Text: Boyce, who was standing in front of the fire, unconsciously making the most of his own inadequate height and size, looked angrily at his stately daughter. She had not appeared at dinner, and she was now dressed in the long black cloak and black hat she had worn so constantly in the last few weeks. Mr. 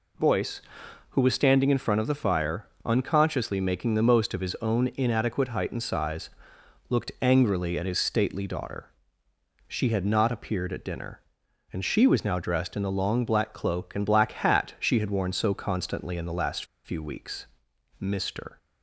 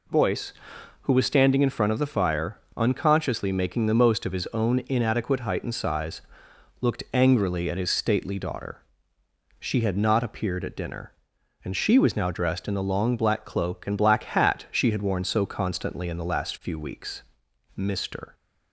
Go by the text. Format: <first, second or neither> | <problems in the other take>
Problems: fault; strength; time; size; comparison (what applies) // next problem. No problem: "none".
second | pauses between "last" and "few"; slight; at 16.6 s; 0.20 s long